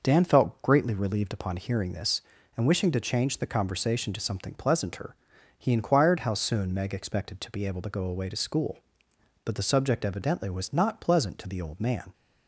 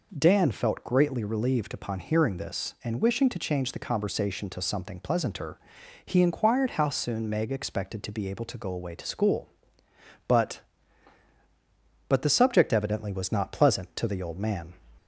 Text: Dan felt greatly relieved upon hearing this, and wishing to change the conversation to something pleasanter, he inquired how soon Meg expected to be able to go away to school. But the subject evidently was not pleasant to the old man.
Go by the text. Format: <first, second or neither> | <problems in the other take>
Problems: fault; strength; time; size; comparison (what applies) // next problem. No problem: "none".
first | says "But" twice; at 12.0 s